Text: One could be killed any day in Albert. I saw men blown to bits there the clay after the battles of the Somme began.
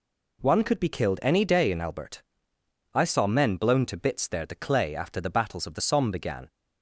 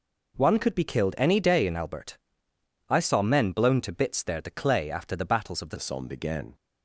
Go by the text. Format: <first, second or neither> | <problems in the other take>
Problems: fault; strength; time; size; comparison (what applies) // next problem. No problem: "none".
first | changes voice at "Somme"; from 5.7 s on; 0.8 s long